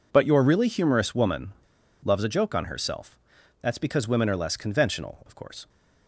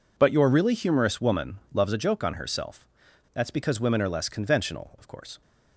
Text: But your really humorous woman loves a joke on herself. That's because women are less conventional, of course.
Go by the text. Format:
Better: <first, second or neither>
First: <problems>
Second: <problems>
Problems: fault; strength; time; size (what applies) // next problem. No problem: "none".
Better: second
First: pauses between "woman" and "loves"; noticeable; at 1.5 s; 0.49 s long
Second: none